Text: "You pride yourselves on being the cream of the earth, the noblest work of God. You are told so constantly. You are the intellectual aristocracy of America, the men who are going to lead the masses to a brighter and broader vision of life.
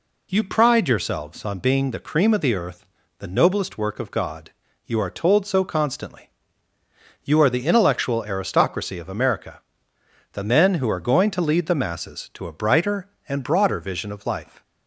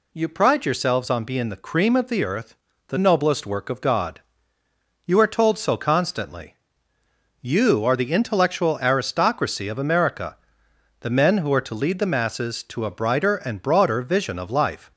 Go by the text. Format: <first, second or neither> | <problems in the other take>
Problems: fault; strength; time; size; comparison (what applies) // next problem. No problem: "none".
first | skips "going"; at 11.6 s